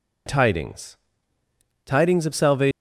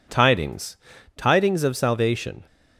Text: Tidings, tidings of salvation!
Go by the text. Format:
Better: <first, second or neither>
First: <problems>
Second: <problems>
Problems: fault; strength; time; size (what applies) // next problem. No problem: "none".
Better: neither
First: none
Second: none